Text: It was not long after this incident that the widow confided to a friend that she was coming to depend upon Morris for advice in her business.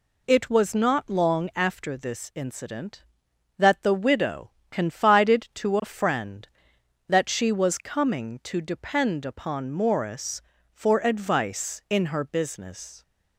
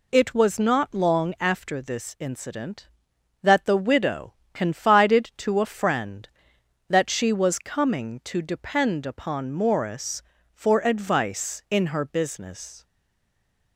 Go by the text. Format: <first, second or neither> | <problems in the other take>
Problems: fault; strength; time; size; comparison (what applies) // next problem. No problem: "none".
first | pauses between "widow" and "confided"; slight; at 4.3 s; 0.18 s long; slight in the first // stays silent after the last word; slight; from 12.8 s on; 0.9 s long